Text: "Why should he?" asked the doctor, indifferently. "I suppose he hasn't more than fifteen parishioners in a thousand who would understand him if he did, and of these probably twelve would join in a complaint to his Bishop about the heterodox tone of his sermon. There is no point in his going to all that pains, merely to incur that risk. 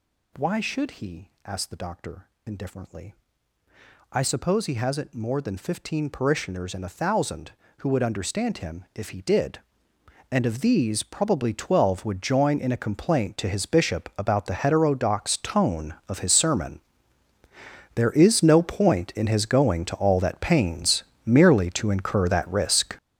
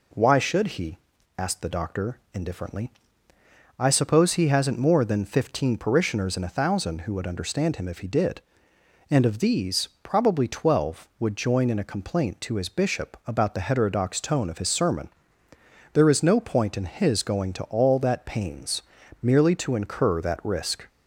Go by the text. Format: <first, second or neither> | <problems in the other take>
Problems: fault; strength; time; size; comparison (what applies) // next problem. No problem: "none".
second | gets louder; strong; throughout; 12 dB